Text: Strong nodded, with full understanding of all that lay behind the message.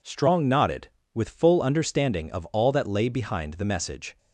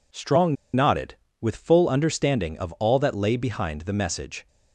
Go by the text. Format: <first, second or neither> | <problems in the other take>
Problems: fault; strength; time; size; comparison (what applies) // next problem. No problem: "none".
first | pauses between "Strong" and "nodded"; slight; at 0.5 s; 0.19 s long